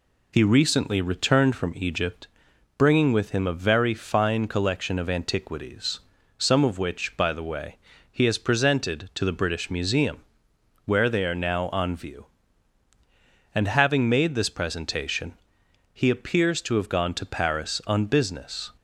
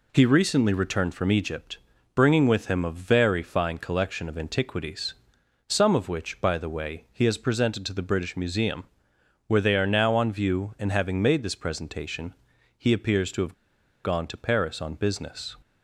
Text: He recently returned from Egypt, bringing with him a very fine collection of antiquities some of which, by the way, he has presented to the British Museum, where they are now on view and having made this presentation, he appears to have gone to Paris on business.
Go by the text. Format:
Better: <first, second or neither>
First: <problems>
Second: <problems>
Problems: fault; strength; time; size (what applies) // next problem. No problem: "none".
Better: first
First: pauses between "antiquities" and "some"; at 5.9 s; 0.40 s long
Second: pauses between "antiquities" and "some"; noticeable; at 5.1 s; 0.58 s long // pauses between "have" and "gone"; noticeable; at 13.5 s; 0.49 s long